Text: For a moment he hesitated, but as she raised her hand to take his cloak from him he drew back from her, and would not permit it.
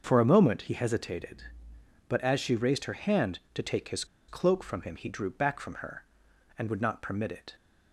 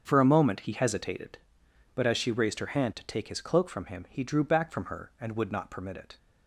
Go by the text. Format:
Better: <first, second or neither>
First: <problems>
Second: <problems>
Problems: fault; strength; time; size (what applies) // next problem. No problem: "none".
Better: second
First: starts louder than the rest; until 1.0 s; 6.5 dB // pauses between "his" and "cloak"; slight; at 4.0 s; 0.23 s long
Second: starts louder than the rest; until 1.0 s; 7 dB